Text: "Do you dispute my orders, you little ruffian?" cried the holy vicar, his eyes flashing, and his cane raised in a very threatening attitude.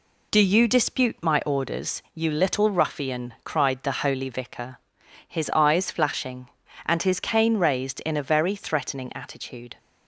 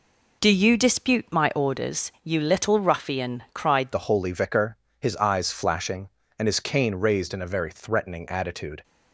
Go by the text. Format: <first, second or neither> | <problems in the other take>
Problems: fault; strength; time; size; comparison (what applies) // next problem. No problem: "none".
first | changes voice at "the"; from 3.9 s on; 4.9 s long